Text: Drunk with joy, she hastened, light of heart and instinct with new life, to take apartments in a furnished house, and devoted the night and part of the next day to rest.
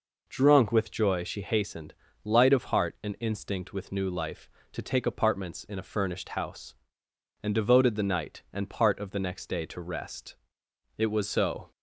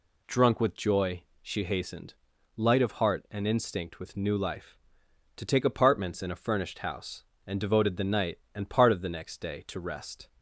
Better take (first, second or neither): second